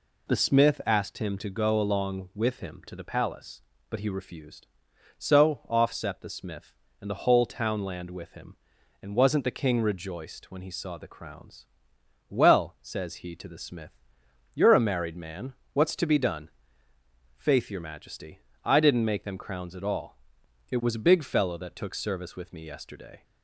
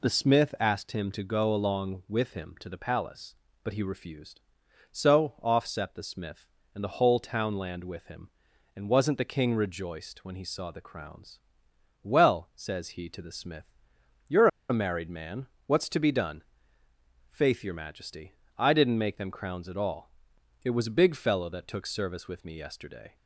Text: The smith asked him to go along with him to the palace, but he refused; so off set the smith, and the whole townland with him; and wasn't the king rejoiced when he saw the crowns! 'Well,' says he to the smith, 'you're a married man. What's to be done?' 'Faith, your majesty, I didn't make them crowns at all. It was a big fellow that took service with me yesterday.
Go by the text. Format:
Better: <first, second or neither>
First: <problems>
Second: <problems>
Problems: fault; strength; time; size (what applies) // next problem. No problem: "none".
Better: first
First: none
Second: pauses between "you're" and "a"; slight; at 14.4 s; 0.22 s long